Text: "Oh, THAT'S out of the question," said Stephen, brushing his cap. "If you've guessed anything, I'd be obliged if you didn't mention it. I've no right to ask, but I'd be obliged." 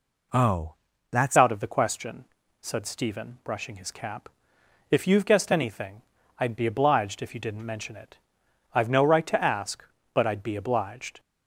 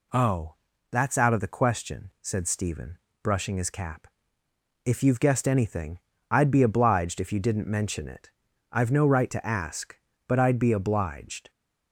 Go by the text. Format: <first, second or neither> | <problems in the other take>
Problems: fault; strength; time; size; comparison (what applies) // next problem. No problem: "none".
second | changes voice at "out"; from 1.3 s on; 9.8 s long